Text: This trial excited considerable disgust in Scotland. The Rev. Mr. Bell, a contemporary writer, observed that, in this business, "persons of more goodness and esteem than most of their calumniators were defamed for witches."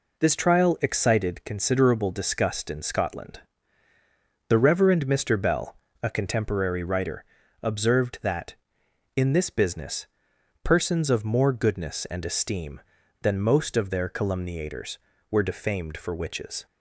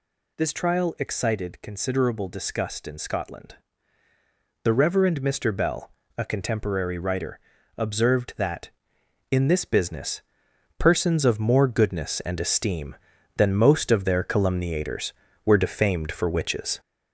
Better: first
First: none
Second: gets louder; noticeable; throughout; 4.5 dB

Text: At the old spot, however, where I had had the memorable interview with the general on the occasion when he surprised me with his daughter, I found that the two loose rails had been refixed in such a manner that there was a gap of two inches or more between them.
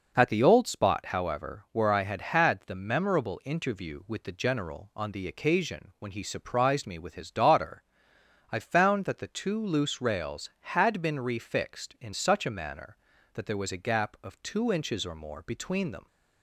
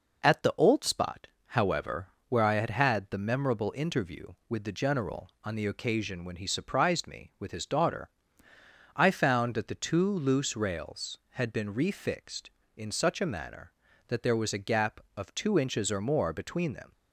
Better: neither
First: none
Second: none

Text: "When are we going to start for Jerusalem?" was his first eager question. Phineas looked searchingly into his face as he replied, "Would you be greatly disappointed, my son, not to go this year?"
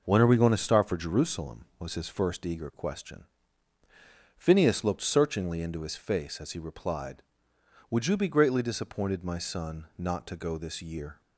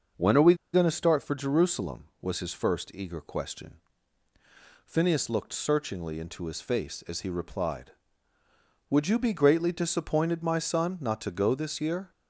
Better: first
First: none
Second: starts louder than the rest; noticeable; until 1.3 s; 6 dB // pauses between "we" and "going"; slight; at 0.5 s; 0.18 s long

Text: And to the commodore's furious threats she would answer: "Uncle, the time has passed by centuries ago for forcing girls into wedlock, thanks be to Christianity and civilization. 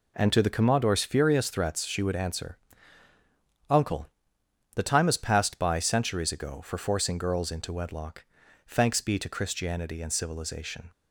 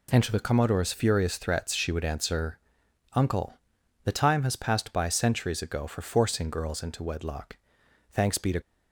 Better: first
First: none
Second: stops before "Christianity and civilization"; at 8.6 s

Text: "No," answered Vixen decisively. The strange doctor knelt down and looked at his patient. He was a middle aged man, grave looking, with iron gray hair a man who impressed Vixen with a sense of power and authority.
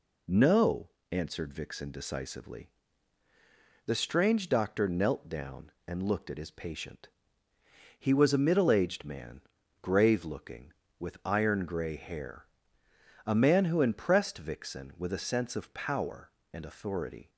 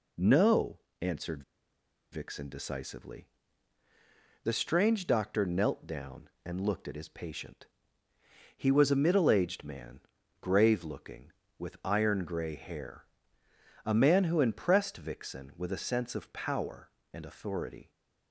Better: first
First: pauses between "hair" and "a"; noticeable; at 12.4 s; 0.80 s long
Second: pauses between "answered" and "Vixen"; noticeable; at 1.4 s; 0.68 s long // pauses between "hair" and "a"; noticeable; at 13.0 s; 0.80 s long

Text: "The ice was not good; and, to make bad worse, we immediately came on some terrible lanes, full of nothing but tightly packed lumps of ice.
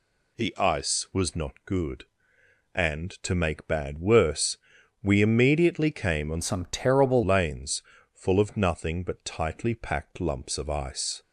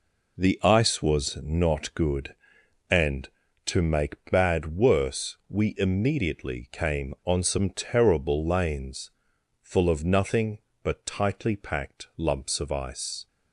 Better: second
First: changes voice from "some" to "terrible"; from 6.4 to 7.2 s; 0.8 s long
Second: none

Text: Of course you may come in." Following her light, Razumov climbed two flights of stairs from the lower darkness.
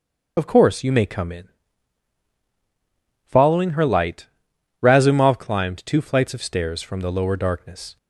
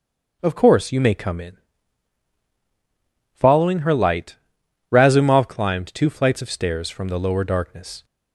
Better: second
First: loses the start of "Of"; at 0.3 s; 55 ms // starts louder than the rest; until 1.3 s; 6 dB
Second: starts louder than the rest; noticeable; until 1.4 s; 6 dB

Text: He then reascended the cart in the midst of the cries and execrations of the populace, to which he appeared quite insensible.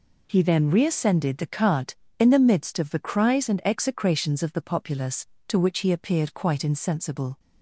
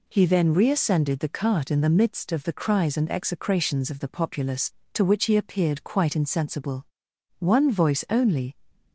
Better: first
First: none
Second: goes on to say "One voice only"; noticeable; from 7.3 s on; 1.1 s long

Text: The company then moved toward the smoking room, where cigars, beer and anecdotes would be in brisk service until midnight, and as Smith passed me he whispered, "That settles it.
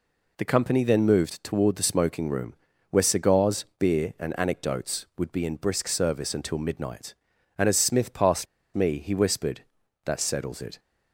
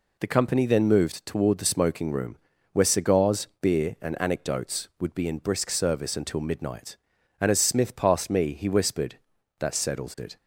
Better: second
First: pauses between "passed" and "me"; slight; at 8.4 s; 0.28 s long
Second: none

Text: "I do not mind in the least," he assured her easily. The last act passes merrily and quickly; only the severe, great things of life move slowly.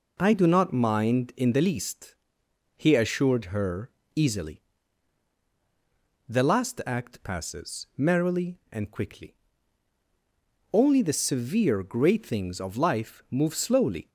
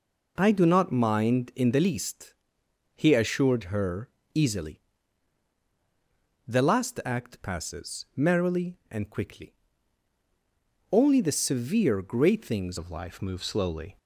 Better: first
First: pauses between "her" and "easily"; slight; at 3.9 s; 0.24 s long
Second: pauses between "her" and "easily"; slight; at 4.0 s; 0.24 s long // changes voice at "of"; from 12.7 s on; 1.2 s long

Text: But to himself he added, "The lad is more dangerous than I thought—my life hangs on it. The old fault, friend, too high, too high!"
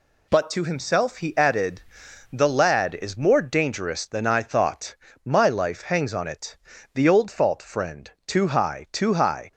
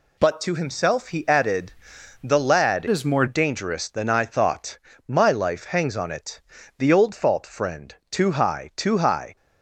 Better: first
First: none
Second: changes voice from "is" to "more"; from 2.8 to 3.2 s; 0.4 s long

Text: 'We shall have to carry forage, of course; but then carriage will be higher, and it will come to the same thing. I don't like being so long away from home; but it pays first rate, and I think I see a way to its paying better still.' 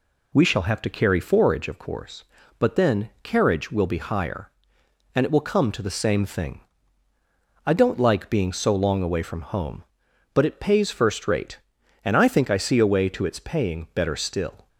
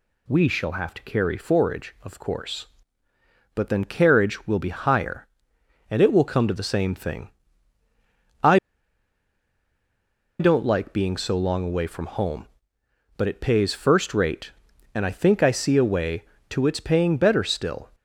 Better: first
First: none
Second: pauses between "I" and "don't"; strong; at 8.5 s; 1.8 s long

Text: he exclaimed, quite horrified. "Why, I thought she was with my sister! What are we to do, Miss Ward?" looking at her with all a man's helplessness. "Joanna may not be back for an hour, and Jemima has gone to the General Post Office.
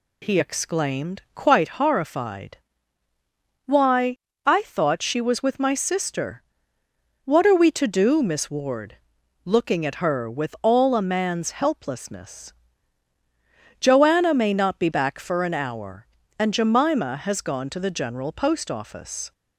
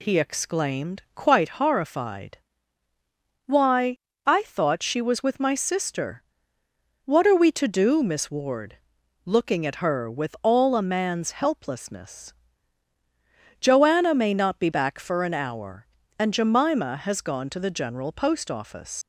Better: first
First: none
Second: leaves "Office" unfinished; at 19.0 s; 100 ms

